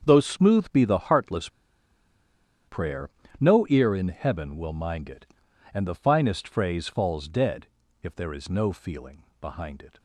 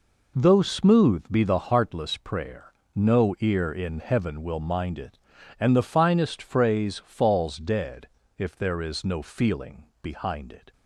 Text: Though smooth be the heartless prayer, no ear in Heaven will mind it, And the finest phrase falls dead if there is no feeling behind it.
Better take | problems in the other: second | starts louder than the rest; until 1.0 s; 7 dB // pauses between "heartless" and "prayer"; at 1.4 s; 1.1 s long // pauses between "dead" and "if"; slight; at 7.6 s; 0.34 s long; slight in the second // pauses between "feeling" and "behind"; slight; at 9.2 s; 0.18 s long; slight in the second

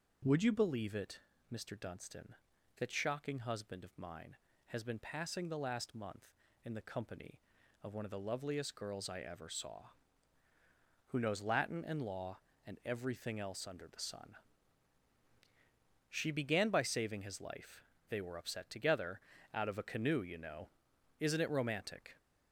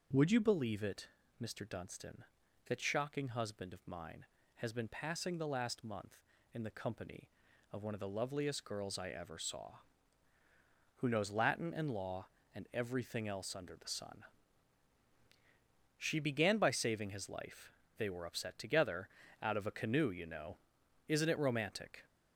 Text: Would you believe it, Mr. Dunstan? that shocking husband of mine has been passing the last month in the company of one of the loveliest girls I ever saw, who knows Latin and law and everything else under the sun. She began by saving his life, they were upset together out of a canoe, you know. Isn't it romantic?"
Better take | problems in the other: neither | pauses between "together" and "out"; slight; the same in both

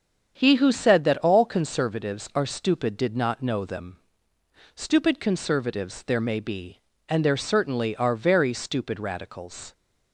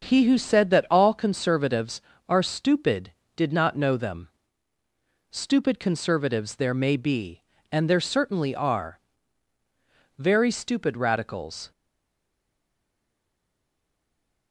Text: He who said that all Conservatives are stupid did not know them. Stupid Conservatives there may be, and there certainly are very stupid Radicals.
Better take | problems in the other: first | starts louder than the rest; until 1.0 s; 6.5 dB; strong in the first // pauses between "are" and "very"; at 8.9 s; 1.1 s long // stays silent after the last word; strong; from 11.7 s on; 2.8 s long

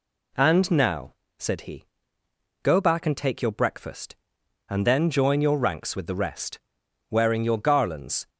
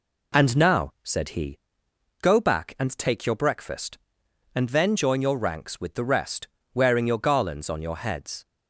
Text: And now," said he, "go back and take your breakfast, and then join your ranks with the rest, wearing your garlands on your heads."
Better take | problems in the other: second | stops before "on your heads"; at 8.2 s

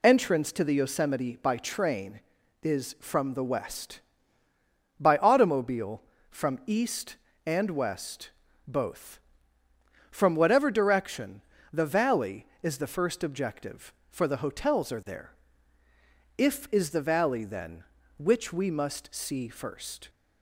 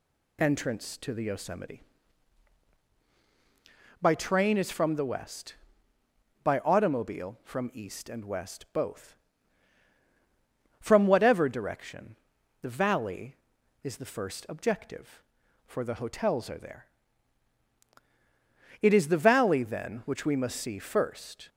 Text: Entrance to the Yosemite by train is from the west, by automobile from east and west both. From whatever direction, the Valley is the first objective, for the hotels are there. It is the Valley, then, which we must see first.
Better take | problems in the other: second | pauses between "west" and "both"; slight; at 8.2 s; 0.36 s long // says "If" for "It"; at 16.3 s

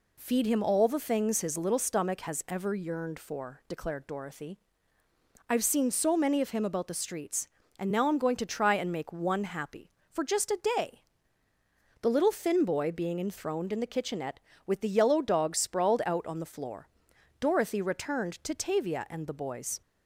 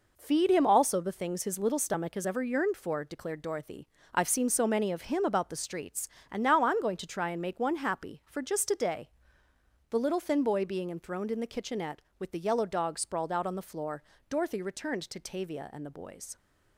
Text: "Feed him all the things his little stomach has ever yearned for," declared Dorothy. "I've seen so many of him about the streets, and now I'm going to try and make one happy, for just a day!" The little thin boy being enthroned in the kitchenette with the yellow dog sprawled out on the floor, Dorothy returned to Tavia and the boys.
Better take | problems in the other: first | says "also" for "all"; at 0.6 s

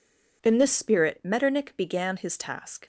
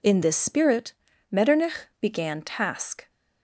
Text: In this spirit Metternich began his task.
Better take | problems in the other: first | pauses between "spirit" and "Metternich"; slight; at 0.9 s; 0.36 s long // skips "his"; at 2.3 s

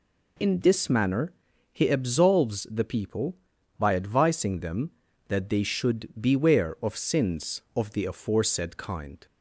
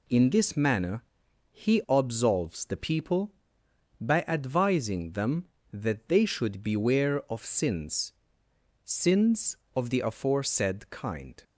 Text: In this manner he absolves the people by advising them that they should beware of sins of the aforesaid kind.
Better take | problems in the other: first | pauses between "manner" and "he"; noticeable; at 1.0 s; 0.50 s long; also in the first // says "sins" twice; at 8.8 s

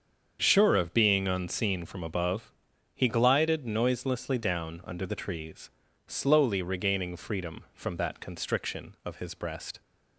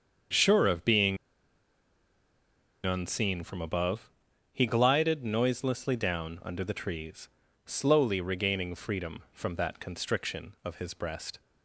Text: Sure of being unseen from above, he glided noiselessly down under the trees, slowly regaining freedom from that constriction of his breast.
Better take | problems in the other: first | starts louder than the rest; strong; until 3.0 s; 7 dB; strong in the first // pauses between "being" and "unseen"; strong; at 1.1 s; 1.6 s long

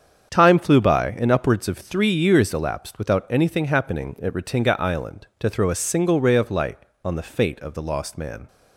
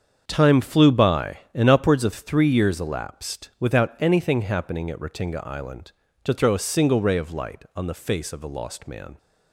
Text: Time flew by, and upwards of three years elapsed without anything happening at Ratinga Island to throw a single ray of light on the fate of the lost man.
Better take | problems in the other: first | starts louder than the rest; strong; until 1.2 s; 7 dB; strong in the first // says "face" for "fate"; at 7.9 s

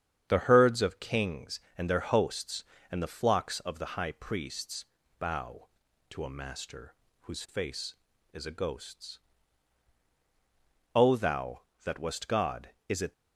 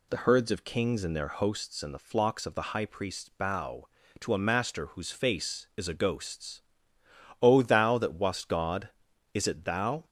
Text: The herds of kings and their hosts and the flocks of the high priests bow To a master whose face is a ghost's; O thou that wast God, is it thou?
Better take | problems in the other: second | starts louder than the rest; strong; until 1.2 s; 8.5 dB // pauses between "priests" and "bow"; slight; at 4.8 s; 0.36 s long // pauses between "master" and "whose"; slight; at 6.9 s; 0.26 s long // stops before "thou"; at 13.1 s

